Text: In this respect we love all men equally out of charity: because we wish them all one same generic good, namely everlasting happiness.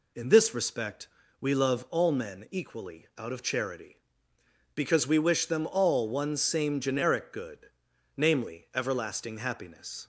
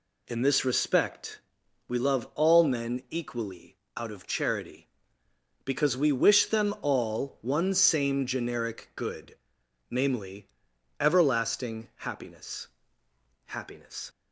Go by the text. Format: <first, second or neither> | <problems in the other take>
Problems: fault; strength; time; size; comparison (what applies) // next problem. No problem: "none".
first | pauses between "respect" and "we"; noticeable; at 1.3 s; 0.48 s long; slight in the first // pauses between "equally" and "out"; slight; at 3.7 s; 0.20 s long // pauses between "namely" and "everlasting"; noticeable; at 10.4 s; 0.52 s long // says "happiness" twice; at 13.4 s